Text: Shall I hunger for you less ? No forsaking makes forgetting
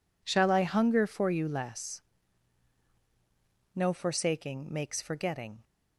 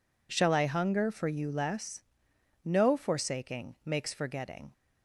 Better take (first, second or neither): neither